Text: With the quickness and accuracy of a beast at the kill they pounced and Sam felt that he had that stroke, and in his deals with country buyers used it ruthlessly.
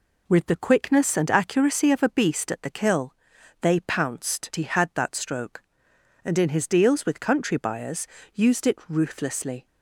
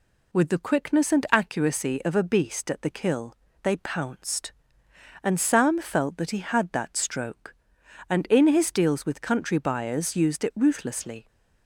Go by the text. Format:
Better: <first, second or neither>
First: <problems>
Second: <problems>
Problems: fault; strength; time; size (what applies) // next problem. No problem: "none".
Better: second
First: pauses between "kill" and "they"; noticeable; at 3.1 s; 0.48 s long // skips "and Sam felt that"; at 4.5 s // pauses between "buyers" and "used"; slight; at 8.0 s; 0.28 s long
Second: pauses between "kill" and "they"; slight; at 3.3 s; 0.28 s long